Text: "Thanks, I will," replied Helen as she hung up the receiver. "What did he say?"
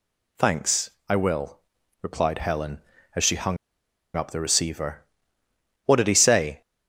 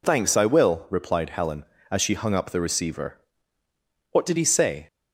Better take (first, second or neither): second